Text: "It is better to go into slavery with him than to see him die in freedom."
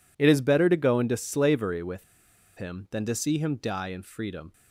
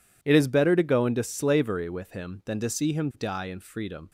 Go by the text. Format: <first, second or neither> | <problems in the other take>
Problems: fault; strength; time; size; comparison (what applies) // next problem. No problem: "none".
second | pauses between "with" and "him"; noticeable; at 2.0 s; 0.52 s long